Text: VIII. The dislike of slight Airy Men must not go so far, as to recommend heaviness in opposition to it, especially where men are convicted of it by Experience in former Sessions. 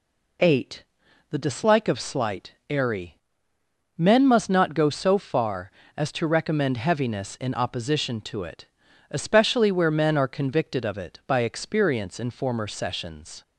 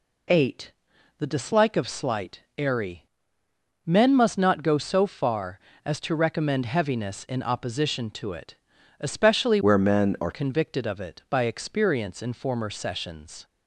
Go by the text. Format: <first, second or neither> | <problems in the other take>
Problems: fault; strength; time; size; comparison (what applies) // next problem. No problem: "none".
first | pauses between "Airy" and "Men"; noticeable; at 3.0 s; 0.80 s long; noticeable in the first // changes voice from "where" to "are"; from 9.6 to 10.3 s; 0.7 s long